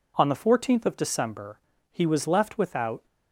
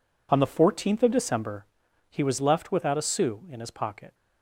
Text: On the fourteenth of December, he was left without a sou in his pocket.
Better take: second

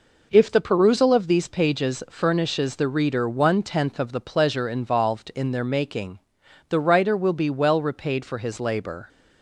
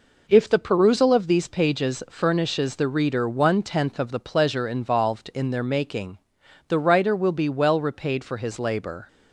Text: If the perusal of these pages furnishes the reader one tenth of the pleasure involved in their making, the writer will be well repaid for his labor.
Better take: neither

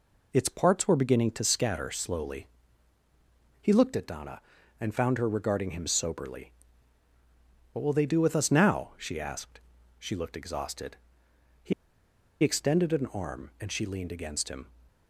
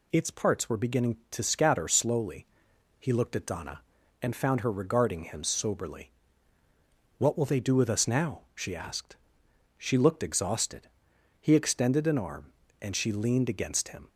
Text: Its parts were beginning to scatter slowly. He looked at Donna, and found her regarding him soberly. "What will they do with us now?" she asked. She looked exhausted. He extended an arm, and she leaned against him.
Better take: second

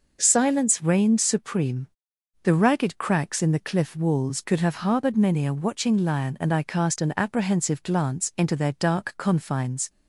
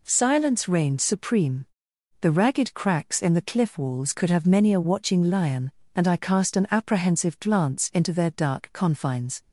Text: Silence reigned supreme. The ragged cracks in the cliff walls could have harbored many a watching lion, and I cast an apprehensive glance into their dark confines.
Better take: first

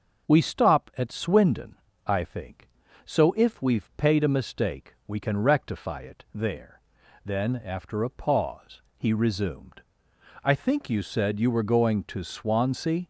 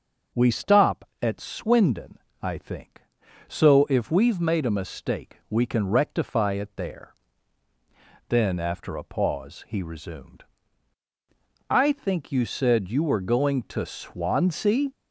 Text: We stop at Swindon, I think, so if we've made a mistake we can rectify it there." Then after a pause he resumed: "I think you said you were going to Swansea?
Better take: second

